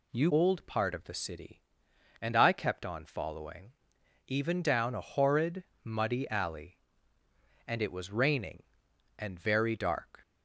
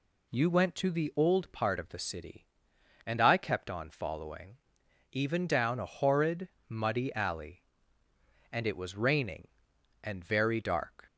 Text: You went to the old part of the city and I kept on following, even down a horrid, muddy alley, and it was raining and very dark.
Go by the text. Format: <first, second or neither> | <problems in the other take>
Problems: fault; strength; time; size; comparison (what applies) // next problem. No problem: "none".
second | skips "went to the"; at 0.3 s